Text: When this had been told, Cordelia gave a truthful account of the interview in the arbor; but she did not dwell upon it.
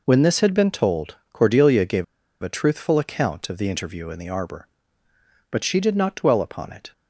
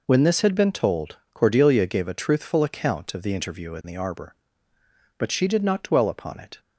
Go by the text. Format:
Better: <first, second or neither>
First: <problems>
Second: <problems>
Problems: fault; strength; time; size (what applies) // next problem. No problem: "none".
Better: second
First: pauses between "gave" and "a"; at 2.0 s; 0.37 s long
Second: none